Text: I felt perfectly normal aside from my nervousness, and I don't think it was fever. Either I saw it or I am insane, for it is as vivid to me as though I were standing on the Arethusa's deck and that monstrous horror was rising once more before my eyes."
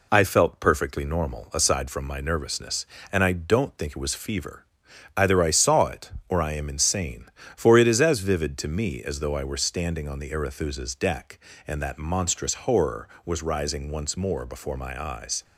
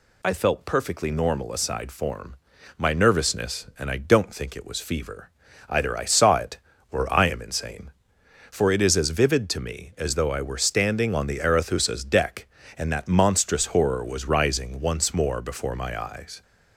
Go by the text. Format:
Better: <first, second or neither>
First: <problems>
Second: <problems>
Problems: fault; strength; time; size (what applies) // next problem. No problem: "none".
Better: first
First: none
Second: says "form" for "from"; at 1.9 s